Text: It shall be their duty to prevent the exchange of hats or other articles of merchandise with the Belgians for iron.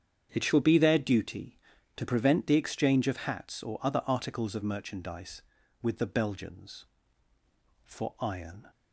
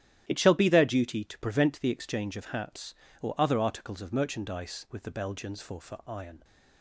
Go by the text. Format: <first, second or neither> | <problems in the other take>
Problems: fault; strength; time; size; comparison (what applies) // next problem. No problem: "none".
first | starts louder than the rest; strong; until 1.2 s; 11.5 dB; strong in the first // says "for" twice; at 5.7 s